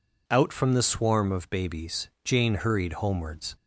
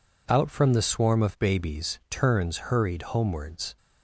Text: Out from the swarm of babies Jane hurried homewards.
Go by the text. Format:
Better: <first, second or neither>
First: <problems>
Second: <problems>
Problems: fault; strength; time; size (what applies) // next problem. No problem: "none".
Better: first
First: none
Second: says "Turns" for "Jane"; at 2.1 s